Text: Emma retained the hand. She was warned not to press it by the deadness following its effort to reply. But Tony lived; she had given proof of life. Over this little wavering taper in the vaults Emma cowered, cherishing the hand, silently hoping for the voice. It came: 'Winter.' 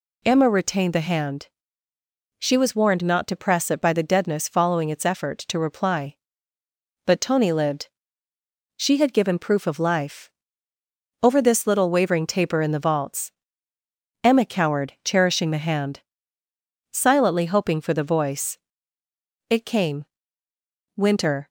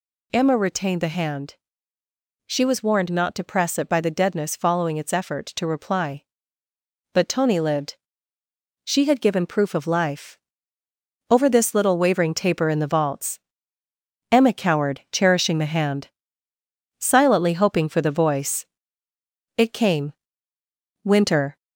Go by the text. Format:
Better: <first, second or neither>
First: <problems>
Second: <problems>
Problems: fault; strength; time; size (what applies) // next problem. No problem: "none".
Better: first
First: pauses between "vaults" and "Emma"; noticeable; at 13.3 s; 0.90 s long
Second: gets louder; throughout; 3.5 dB // pauses between "vaults" and "Emma"; noticeable; at 13.3 s; 0.90 s long